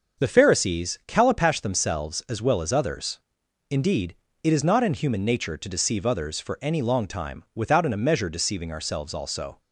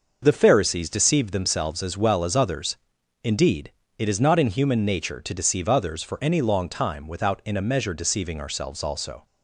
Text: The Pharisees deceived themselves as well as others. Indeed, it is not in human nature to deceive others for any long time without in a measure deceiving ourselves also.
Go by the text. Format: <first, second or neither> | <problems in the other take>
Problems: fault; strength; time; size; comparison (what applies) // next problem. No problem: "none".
second | starts louder than the rest; until 1.2 s; 6.5 dB // says "calipash" for "deceived"; at 1.0 s